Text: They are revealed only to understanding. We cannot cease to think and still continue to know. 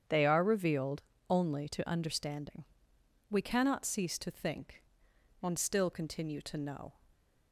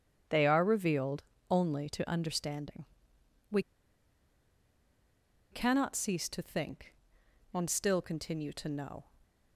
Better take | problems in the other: first | starts louder than the rest; strong; until 1.5 s; 8.5 dB; strong in the first // pauses between "revealed" and "only"; slight; at 1.2 s; 0.26 s long; slight in the first // pauses between "We" and "cannot"; strong; at 3.6 s; 1.9 s long

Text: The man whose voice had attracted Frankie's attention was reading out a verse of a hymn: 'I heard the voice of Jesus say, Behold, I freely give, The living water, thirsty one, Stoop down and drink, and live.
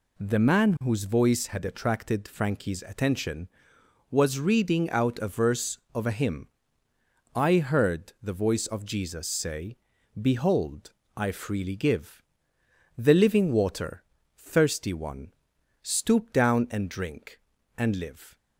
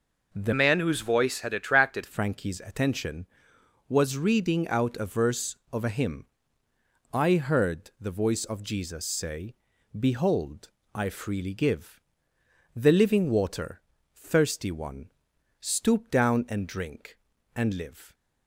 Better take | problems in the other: first | changes voice from "man" to "attracted"; from 0.5 to 2.0 s; 1.5 s long

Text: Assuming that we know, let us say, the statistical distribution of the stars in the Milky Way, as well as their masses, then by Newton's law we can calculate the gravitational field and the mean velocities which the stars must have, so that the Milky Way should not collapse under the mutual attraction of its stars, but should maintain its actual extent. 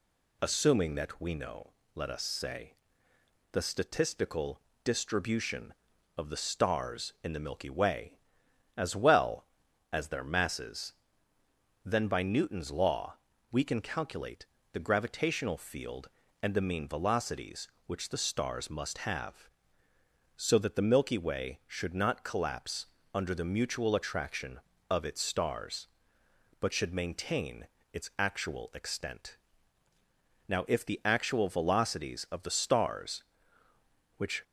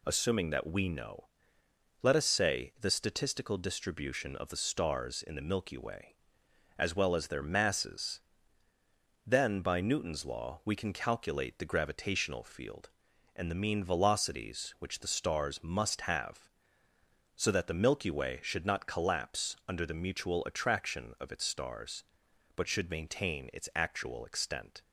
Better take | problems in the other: second | pauses between "statistical" and "distribution"; slight; at 4.6 s; 0.24 s long // pauses between "law" and "we"; slight; at 13.1 s; 0.36 s long // pauses between "calculate" and "the"; slight; at 14.4 s; 0.26 s long // pauses between "collapse" and "under"; slight; at 22.8 s; 0.28 s long // pauses between "maintain" and "its"; slight; at 27.6 s; 0.26 s long // goes on to say "Now if the actual velocities of the stars which"; strong; from 30.4 s on; 3.9 s long

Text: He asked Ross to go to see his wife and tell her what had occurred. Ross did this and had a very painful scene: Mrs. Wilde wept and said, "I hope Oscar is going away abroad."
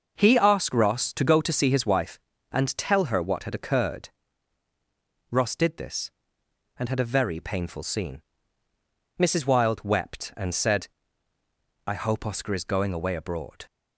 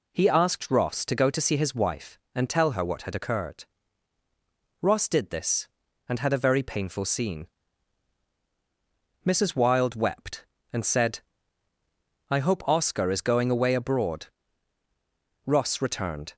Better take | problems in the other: first | goes on to say "Ross returned"; noticeable; from 15.4 s on; 0.90 s long

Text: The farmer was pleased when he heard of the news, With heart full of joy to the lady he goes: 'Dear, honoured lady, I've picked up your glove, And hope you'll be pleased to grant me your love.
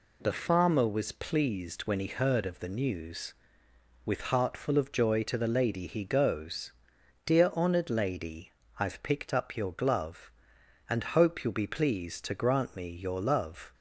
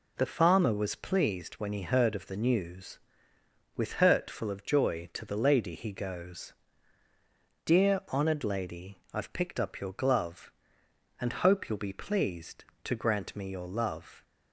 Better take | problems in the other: first | says "hurt" for "heart"; at 3.9 s

